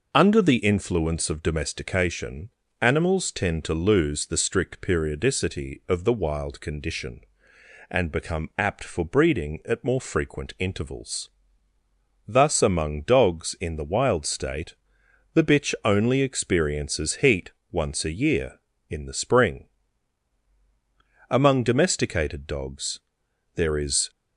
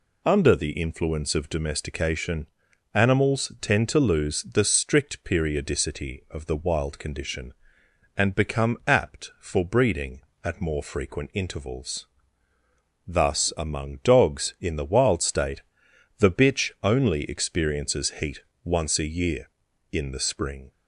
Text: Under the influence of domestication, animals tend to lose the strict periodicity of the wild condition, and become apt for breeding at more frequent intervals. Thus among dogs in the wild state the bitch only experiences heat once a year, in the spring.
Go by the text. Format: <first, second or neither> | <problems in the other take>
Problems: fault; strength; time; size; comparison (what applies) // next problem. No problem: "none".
second | pauses between "state" and "the"; noticeable; at 14.7 s; 0.60 s long; noticeable in the second // pauses between "heat" and "once"; slight; at 17.5 s; 0.18 s long; slight in the second // goes on to say "Among domesticated dogs there is"; strong; from 21.2 s on; 2.8 s long